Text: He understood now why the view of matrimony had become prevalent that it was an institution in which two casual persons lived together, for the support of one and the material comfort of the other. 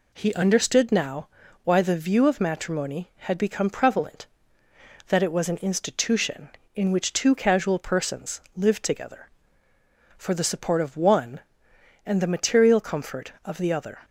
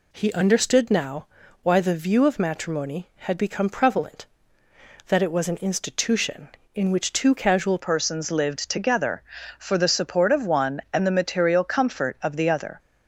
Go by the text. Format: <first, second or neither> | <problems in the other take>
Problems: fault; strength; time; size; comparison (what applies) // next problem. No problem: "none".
first | pauses between "now" and "why"; slight; at 1.2 s; 0.36 s long; slight in the first // changes voice at "persons"; from 7.8 s on; 4.9 s long